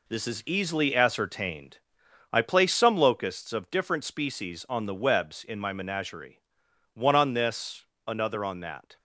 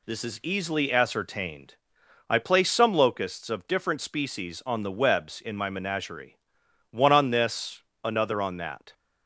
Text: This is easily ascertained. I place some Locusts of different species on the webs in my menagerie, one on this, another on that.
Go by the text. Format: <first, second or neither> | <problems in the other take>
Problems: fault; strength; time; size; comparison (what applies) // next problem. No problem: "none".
second | gets quieter; throughout; 6.5 dB